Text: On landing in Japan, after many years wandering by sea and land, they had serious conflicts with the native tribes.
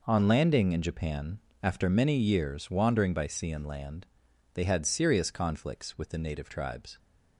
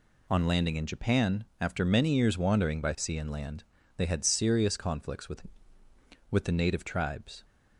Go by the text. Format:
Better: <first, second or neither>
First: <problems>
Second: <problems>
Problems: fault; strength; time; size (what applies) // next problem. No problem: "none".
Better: first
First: none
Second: says "with" twice; at 6.3 s